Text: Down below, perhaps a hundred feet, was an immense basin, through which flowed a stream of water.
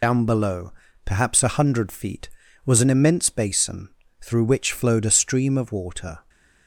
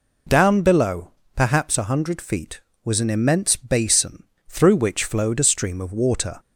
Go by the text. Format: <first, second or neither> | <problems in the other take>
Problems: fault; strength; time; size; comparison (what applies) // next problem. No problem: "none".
second | loses the start of "Down"; at 0.0 s; 50 ms